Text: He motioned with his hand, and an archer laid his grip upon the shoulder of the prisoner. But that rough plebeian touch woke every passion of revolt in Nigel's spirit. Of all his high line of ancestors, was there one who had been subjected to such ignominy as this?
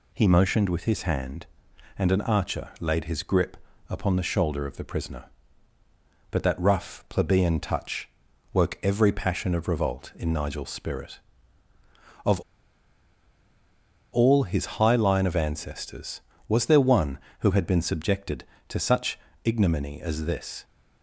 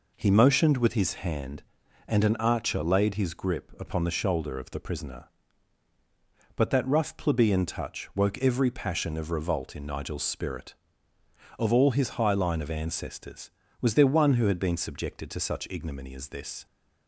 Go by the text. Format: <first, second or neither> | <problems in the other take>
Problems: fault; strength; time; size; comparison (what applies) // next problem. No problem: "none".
second | pauses between "grip" and "upon"; slight; at 3.5 s; 0.32 s long // pauses between "touch" and "woke"; at 8.0 s; 0.44 s long // pauses between "Of" and "all"; strong; at 12.3 s; 1.7 s long // pauses between "such" and "ignominy"; slight; at 19.1 s; 0.26 s long